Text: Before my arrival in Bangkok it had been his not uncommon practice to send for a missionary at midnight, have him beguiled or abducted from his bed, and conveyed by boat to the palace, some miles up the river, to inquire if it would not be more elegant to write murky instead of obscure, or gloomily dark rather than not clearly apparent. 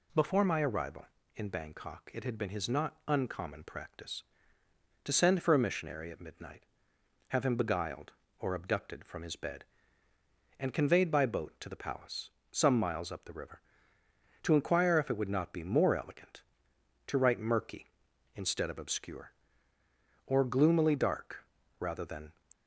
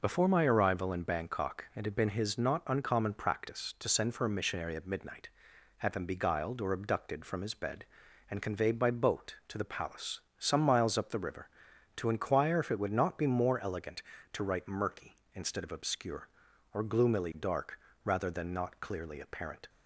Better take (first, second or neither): second